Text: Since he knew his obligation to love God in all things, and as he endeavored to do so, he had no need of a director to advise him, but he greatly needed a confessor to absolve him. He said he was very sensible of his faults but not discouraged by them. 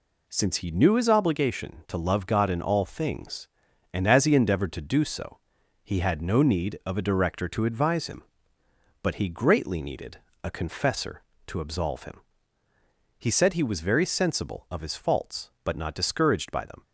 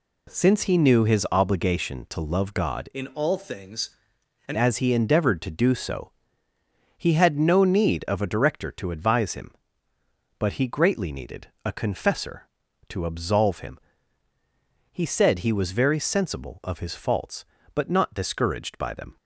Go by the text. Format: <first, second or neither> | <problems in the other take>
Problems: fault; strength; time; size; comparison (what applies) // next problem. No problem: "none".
first | changes voice from "in" to "and"; from 2.9 to 4.5 s; 1.6 s long // pauses between "needed" and "a"; slight; at 11.4 s; 0.18 s long; slight in the first